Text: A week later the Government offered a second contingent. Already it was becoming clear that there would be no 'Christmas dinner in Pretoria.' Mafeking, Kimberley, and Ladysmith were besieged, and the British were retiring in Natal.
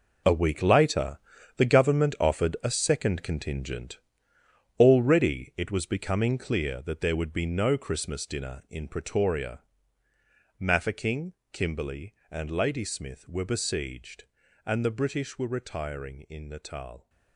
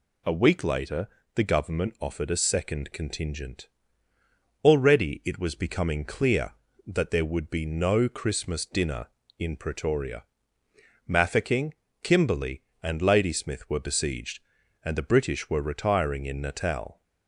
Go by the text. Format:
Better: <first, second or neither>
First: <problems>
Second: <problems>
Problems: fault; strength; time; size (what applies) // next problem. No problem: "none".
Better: second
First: gets quieter; strong; throughout; 12 dB // pauses between "later" and "the"; at 1.1 s; 0.40 s long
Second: pauses between "later" and "the"; slight; at 1.0 s; 0.28 s long